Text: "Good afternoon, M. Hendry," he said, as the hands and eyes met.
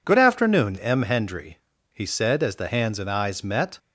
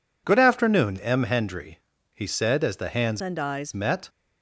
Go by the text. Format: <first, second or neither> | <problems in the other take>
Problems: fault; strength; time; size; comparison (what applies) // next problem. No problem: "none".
first | changes voice from "and" to "eyes"; from 3.1 to 3.7 s; 0.6 s long